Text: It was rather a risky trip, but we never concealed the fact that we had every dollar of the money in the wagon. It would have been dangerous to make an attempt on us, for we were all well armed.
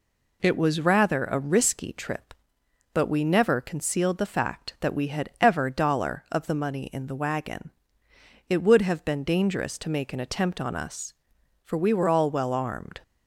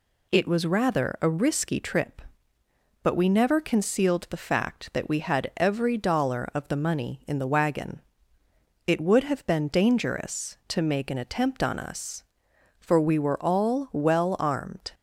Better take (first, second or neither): second